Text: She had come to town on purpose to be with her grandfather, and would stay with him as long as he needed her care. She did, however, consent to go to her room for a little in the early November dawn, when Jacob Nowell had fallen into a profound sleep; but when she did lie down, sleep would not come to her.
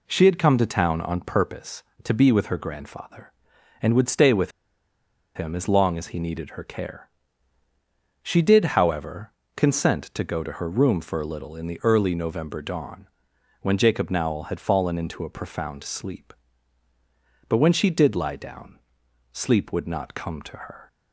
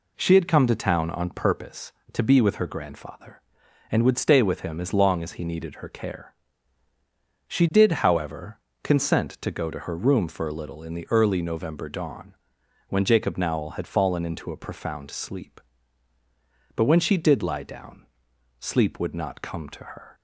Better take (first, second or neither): second